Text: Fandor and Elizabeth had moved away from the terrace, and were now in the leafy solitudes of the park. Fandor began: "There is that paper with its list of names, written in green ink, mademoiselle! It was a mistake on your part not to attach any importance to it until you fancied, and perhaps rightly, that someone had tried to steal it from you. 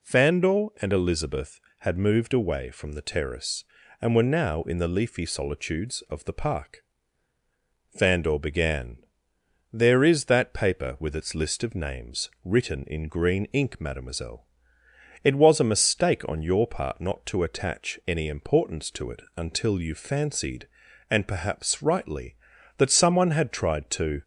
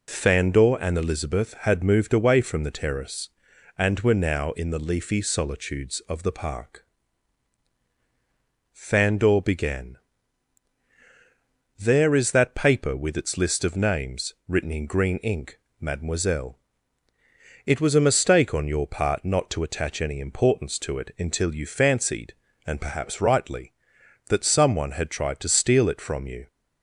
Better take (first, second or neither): second